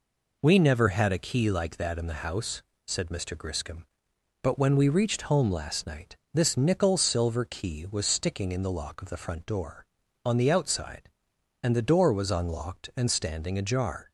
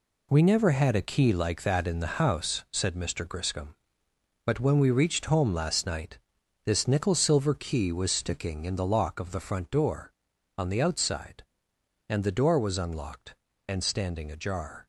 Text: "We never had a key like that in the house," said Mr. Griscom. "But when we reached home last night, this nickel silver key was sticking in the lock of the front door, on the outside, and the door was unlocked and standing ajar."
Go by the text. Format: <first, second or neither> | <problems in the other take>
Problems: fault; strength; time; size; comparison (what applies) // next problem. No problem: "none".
first | gets quieter; strong; throughout; 8 dB